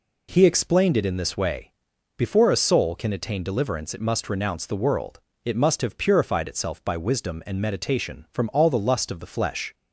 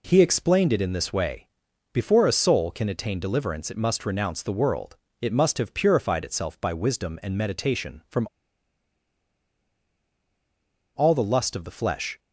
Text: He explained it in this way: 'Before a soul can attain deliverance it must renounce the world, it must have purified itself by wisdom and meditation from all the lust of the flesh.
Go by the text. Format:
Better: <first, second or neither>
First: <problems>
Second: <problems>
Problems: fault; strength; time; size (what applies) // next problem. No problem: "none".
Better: first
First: none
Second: pauses between "from" and "all"; strong; at 8.2 s; 2.6 s long